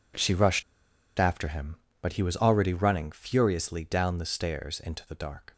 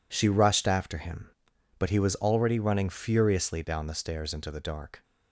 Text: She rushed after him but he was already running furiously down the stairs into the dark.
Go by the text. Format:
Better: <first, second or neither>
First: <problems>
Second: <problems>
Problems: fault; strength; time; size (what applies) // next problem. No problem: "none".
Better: second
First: pauses between "rushed" and "after"; noticeable; at 0.6 s; 0.55 s long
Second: none